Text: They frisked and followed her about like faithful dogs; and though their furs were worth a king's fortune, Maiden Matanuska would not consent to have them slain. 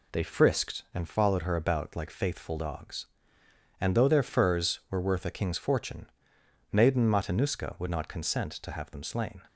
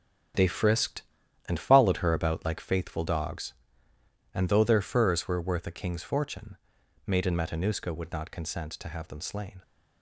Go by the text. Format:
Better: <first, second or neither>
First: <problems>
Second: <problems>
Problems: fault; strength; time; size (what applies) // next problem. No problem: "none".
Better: first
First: none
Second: gets quieter; strong; throughout; 10 dB